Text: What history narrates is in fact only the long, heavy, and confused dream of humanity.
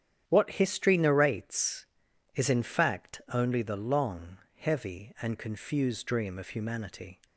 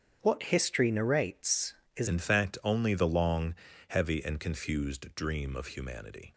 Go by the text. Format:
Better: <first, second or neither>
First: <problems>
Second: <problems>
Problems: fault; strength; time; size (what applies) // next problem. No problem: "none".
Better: first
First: starts louder than the rest; strong; until 1.2 s; 9.5 dB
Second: starts louder than the rest; strong; until 1.2 s; 8 dB // changes voice at "in"; from 2.0 s on; 4.3 s long